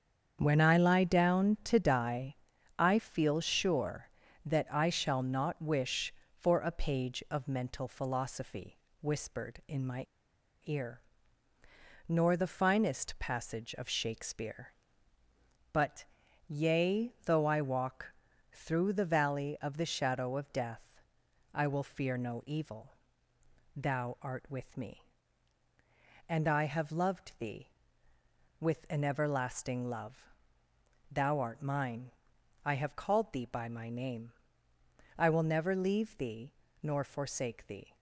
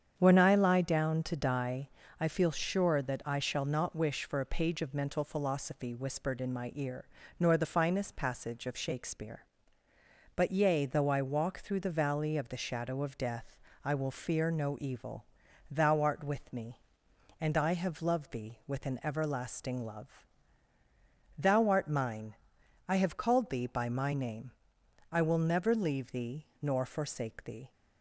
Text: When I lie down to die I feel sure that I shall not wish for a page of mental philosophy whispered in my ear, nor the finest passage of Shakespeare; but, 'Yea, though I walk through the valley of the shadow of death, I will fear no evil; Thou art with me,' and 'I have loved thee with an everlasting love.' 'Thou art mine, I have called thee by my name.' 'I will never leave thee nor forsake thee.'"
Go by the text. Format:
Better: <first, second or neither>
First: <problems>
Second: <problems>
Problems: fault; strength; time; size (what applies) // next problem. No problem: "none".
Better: second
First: starts louder than the rest; strong; until 1.4 s; 7.5 dB // pauses between "die" and "I"; at 2.3 s; 0.42 s long // pauses between "philosophy" and "whispered"; slight; at 8.7 s; 0.24 s long // pauses between "my" and "ear"; noticeable; at 10.0 s; 0.59 s long // pauses between "walk" and "through"; at 18.1 s; 0.40 s long // pauses between "thee" and "nor"; slight; at 36.5 s; 0.30 s long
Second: starts louder than the rest; strong; until 1.1 s; 8 dB // pauses between "die" and "I"; slight; at 1.8 s; 0.32 s long